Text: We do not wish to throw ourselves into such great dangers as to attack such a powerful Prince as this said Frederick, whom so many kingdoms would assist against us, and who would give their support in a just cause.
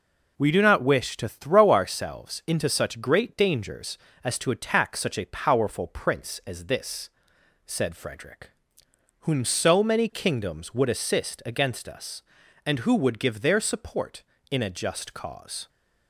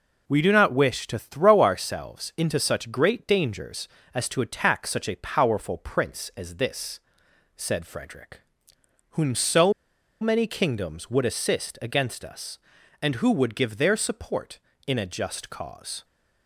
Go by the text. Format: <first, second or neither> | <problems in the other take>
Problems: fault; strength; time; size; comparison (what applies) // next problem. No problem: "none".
first | pauses between "this" and "said"; noticeable; at 6.9 s; 0.58 s long; noticeable in the first // pauses between "so" and "many"; noticeable; at 9.7 s; 0.49 s long